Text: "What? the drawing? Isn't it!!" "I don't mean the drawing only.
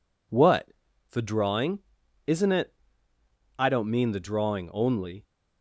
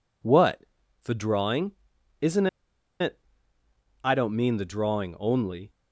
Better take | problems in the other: first | pauses between "Isn't" and "it"; noticeable; at 2.4 s; 0.53 s long

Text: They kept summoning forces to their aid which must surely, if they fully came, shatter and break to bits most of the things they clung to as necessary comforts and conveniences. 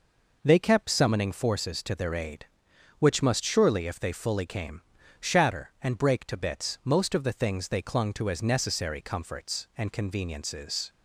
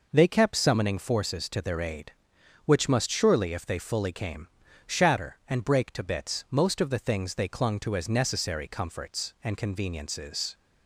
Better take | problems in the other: neither | none

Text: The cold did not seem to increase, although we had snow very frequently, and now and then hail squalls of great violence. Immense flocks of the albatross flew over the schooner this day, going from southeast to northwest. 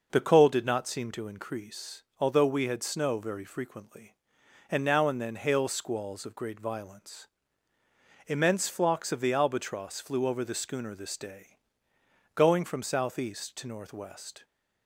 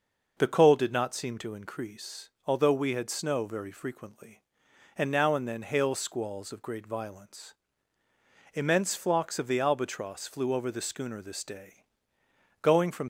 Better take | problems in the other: first | stops before "southeast to northwest"; at 13.0 s

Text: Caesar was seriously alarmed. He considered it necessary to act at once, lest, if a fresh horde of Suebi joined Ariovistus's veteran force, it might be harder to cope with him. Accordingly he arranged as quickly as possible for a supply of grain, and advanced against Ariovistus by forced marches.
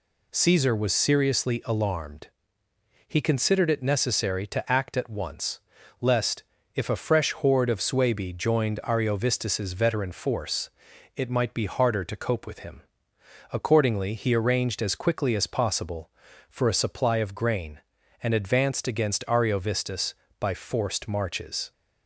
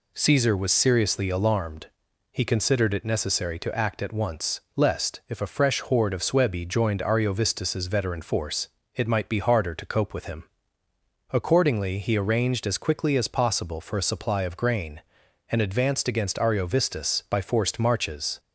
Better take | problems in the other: neither | none

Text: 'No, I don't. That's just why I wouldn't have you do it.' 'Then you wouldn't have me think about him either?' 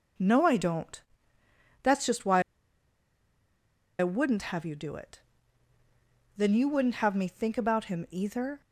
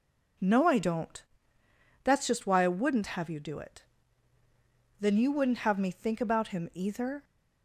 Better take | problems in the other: second | pauses between "why" and "I"; strong; at 2.4 s; 1.5 s long

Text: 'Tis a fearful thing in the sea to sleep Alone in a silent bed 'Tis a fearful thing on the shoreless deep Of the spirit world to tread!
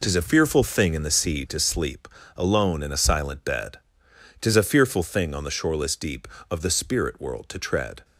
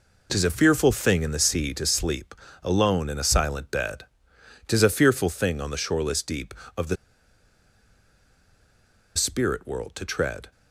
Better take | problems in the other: first | pauses between "sleep" and "Alone"; slight; at 2.3 s; 0.30 s long; slight in the first // pauses between "bed" and "Tis"; noticeable; at 4.0 s; 0.64 s long; noticeable in the first // pauses between "the" and "spirit"; strong; at 6.9 s; 2.2 s long

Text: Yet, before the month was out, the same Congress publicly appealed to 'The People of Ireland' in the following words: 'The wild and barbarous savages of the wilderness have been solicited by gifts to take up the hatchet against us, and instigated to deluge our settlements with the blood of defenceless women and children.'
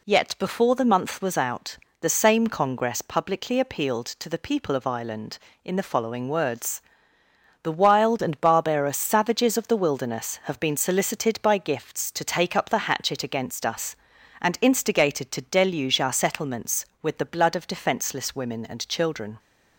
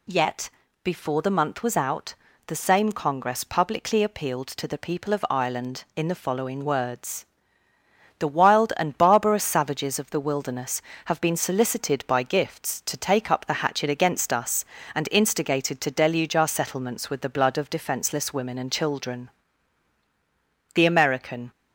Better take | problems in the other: first | goes on to say "The American"; noticeable; from 20.7 s on; 0.78 s long

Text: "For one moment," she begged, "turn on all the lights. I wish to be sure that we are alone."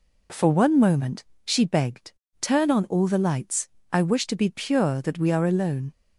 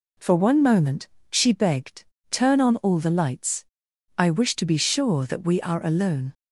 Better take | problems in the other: second | says "pure" for "sure"; at 4.5 s

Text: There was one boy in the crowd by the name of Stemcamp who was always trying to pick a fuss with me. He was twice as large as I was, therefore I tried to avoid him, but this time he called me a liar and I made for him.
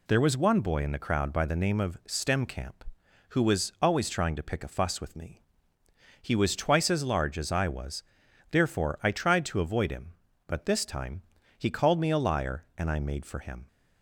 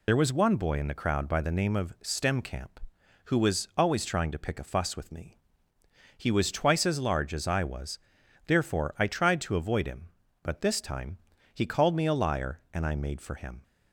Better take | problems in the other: first | loses the start of "There"; at 0.0 s; 45 ms // pauses between "time" and "he"; slight; at 11.1 s; 0.36 s long; slight in the first

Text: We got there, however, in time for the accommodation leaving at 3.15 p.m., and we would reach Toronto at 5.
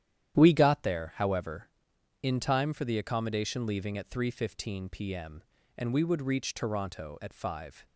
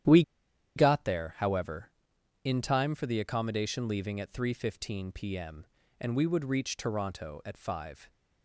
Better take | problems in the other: first | starts louder than the rest; strong; until 1.6 s; 10.5 dB; strong in the first // pauses between "We" and "got"; noticeable; at 0.2 s; 0.54 s long

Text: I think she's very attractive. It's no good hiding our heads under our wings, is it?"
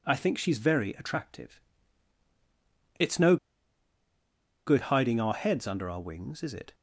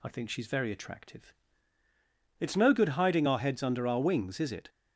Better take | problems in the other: second | pauses between "no" and "good"; strong; at 3.3 s; 1.3 s long

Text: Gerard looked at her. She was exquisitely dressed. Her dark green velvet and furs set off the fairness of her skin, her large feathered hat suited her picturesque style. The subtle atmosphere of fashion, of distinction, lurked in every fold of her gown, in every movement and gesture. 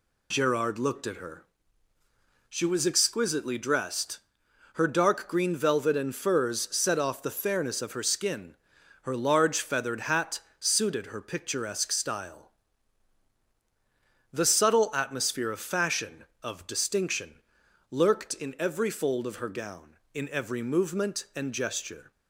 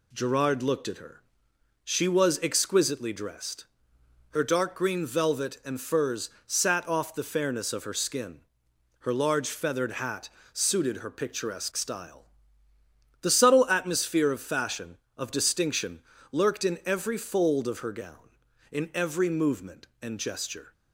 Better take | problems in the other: first | says "sat" for "set"; at 6.4 s // pauses between "hat" and "suited"; slight; at 10.2 s; 0.24 s long; slight in the first

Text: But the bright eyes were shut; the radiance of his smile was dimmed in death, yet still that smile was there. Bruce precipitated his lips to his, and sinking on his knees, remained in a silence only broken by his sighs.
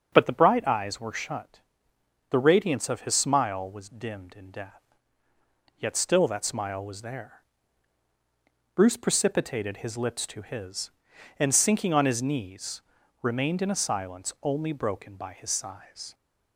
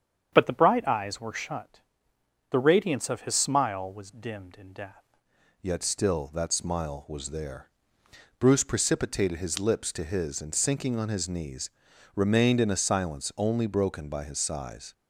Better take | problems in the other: first | starts louder than the rest; strong; until 1.3 s; 8 dB; strong in the first // changes voice at "yet"; from 5.6 s on; 9.3 s long

